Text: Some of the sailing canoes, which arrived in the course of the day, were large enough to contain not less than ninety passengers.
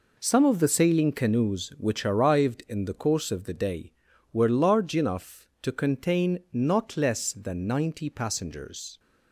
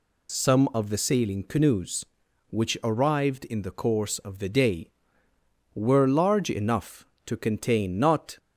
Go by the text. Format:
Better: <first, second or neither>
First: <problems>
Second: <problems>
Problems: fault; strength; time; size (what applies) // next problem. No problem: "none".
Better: first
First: none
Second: stops before "less than ninety passengers"; at 8.3 s